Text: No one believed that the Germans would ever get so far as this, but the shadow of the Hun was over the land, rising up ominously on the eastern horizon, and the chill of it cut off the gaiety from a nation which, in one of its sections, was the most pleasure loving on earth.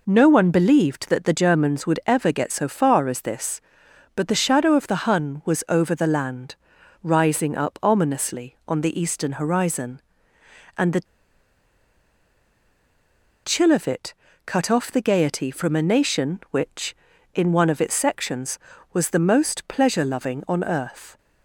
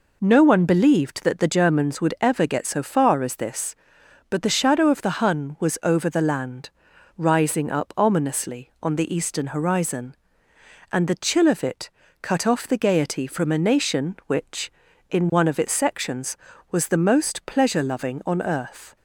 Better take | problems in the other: second | pauses between "the" and "chill"; strong; at 11.0 s; 2.3 s long // pauses between "it" and "cut"; slight; at 14.1 s; 0.32 s long; slight in the second

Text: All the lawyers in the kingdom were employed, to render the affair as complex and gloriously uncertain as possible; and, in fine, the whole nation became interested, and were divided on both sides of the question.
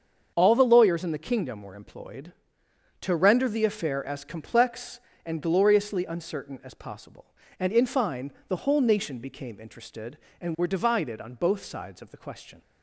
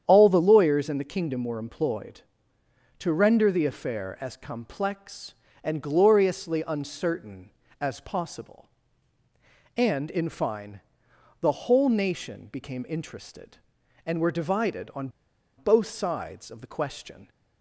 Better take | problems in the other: first | starts louder than the rest; strong; until 1.0 s; 9 dB; also in the first // pauses between "on" and "both"; noticeable; at 15.0 s; 0.49 s long

